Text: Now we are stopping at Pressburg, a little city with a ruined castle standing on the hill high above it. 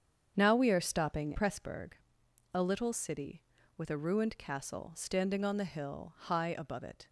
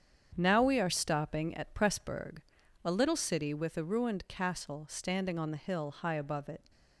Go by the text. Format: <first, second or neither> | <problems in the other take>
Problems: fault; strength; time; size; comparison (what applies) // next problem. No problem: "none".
second | starts louder than the rest; strong; until 1.3 s; 7.5 dB; strong in the second // skips "at"; at 1.3 s